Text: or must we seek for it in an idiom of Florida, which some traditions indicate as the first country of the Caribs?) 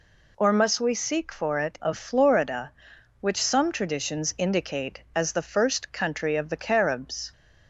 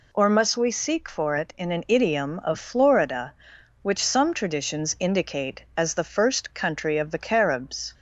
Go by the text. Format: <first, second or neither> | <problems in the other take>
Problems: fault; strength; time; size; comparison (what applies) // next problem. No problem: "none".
second | skips "in an idiom"; at 1.8 s